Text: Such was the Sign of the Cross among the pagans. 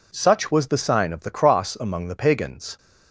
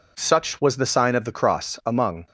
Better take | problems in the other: first | stops before "the pagans"; at 2.2 s

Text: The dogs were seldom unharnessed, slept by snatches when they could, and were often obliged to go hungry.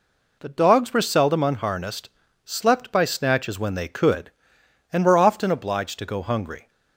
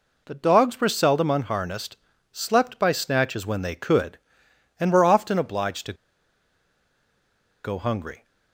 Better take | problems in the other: first | pauses between "to" and "go"; strong; at 5.9 s; 1.6 s long

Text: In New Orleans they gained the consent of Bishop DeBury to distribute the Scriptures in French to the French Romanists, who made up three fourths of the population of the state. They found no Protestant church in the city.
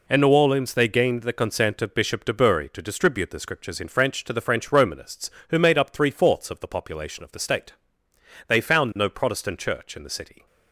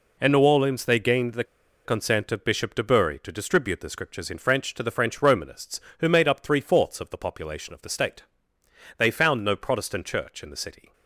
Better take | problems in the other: first | pauses between "the" and "consent"; at 1.4 s; 0.41 s long

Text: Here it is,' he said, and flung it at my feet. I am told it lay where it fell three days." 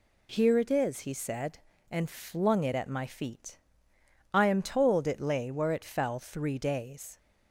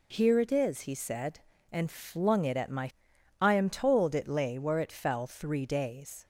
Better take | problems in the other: first | skips "feet"; at 3.1 s

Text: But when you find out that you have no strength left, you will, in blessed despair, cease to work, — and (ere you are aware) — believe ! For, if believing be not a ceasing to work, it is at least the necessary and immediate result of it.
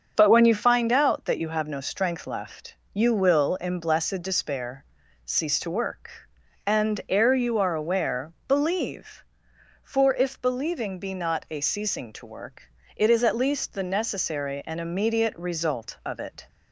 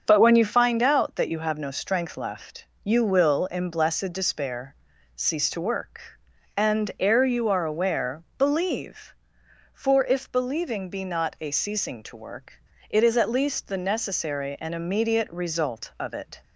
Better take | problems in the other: neither | starts louder than the rest; the same in both

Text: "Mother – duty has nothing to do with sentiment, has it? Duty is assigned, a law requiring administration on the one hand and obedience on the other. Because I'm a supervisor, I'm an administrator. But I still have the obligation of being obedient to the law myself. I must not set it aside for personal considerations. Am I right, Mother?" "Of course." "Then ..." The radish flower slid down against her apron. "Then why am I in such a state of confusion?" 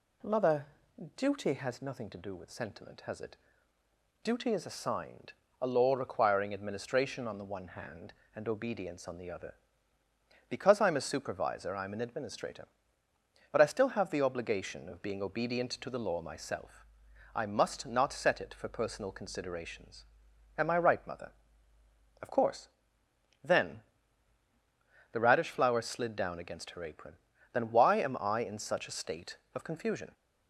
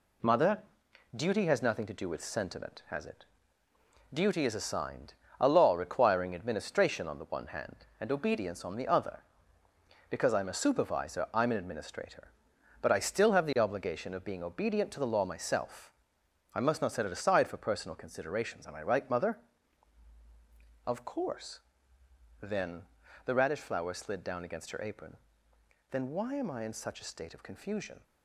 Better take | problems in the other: second | skips "aside"; at 18.5 s

